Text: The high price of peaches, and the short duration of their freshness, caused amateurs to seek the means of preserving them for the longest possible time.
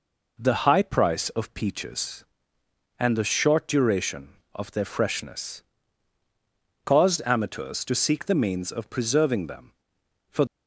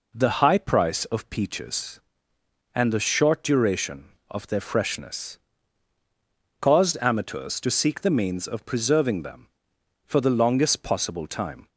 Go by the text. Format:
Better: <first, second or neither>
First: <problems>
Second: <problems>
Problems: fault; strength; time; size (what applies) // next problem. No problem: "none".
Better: second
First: stops before "the longest possible time"; at 10.4 s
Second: none